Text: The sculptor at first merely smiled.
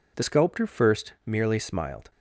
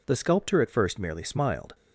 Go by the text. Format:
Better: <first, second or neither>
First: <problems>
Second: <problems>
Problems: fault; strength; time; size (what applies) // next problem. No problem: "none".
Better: second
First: skips "at"; at 0.6 s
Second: none